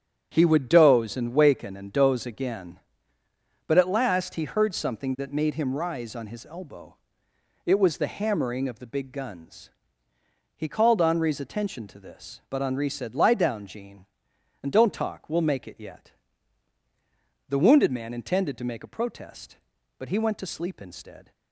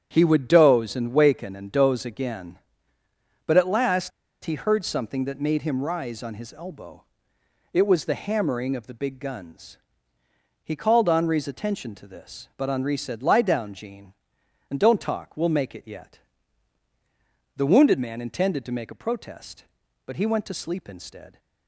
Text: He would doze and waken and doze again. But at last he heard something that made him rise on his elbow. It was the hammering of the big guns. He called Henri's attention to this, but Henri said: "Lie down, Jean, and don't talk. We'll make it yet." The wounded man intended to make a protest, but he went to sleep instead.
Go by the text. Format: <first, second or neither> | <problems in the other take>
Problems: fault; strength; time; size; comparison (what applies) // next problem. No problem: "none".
first | starts louder than the rest; strong; until 1.1 s; 9 dB; strong in the first // pauses between "last" and "he"; slight; at 4.1 s; 0.32 s long